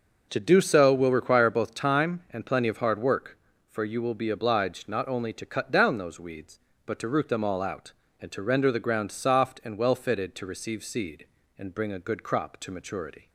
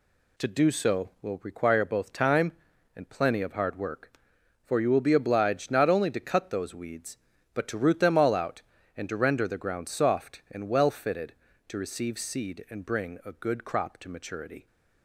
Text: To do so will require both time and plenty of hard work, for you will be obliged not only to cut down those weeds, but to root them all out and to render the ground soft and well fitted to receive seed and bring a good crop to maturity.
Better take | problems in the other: first | skips "down"; at 6.4 s

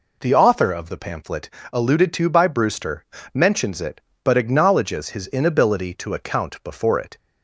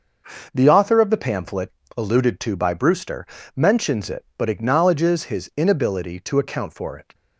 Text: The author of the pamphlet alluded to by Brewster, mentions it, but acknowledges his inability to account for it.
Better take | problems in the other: second | pauses between "pamphlet" and "alluded"; slight; at 1.4 s; 0.24 s long; slight in the second // says "before" for "for"; at 6.6 s

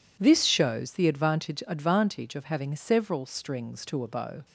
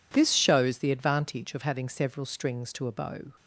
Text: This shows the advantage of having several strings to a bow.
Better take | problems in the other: second | says "advantage" twice; at 1.6 s

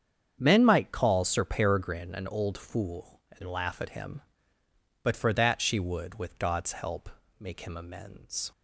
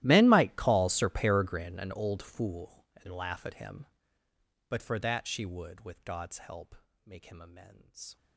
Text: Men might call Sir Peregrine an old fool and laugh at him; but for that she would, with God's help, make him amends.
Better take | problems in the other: first | gets quieter; strong; throughout; 23.5 dB // starts louder than the rest; strong; until 1.0 s; 14.5 dB; strong in the first

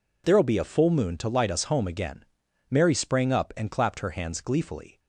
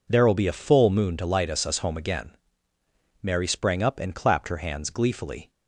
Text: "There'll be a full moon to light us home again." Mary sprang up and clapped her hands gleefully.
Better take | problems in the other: first | says "us" twice; at 1.6 s

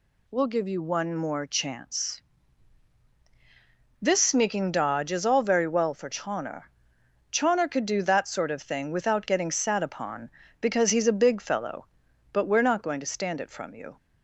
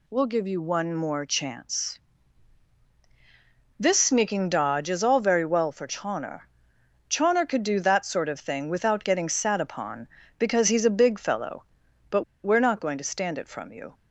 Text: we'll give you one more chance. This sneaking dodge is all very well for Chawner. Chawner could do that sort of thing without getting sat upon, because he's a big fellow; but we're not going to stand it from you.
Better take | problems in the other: first | pauses between "but" and "we're"; slight; at 12.2 s; 0.20 s long

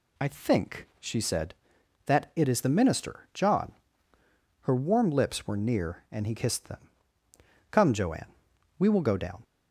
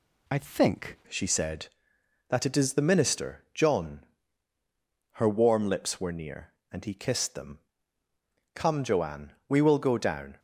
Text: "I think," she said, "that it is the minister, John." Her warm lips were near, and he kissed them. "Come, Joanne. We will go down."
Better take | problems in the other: first | changes voice at "she"; from 1.0 s on; 9.3 s long

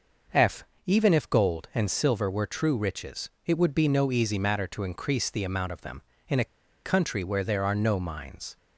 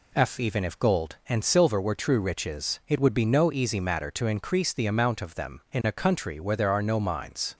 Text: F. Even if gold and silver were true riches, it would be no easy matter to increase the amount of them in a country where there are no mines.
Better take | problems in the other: second | pauses between "a" and "country"; at 6.4 s; 0.39 s long

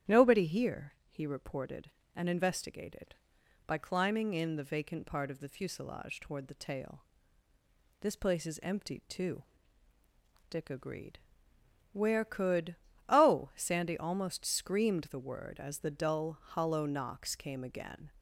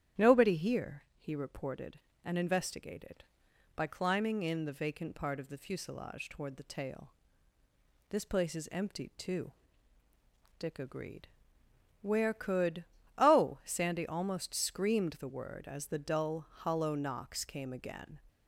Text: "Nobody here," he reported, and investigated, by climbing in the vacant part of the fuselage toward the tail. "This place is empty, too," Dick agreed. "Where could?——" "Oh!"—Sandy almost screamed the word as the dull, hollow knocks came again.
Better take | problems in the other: neither | starts louder than the rest; strong; the same in both

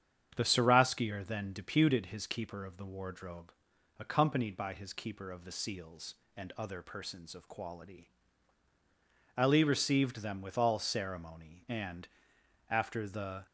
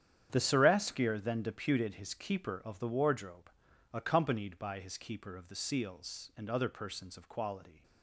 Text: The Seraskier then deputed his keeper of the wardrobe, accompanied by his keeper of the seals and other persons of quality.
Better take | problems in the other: second | starts louder than the rest; strong; until 1.3 s; 8 dB; strong in the second // goes on to say "Ali received them with all ceremony and after the"; strong; from 9.3 s on; 4.0 s long

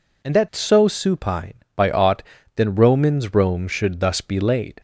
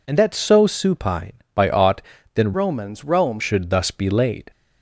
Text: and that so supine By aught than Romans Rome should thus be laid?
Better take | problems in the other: first | changes voice from "Romans" to "Rome"; from 2.5 to 3.4 s; 0.9 s long

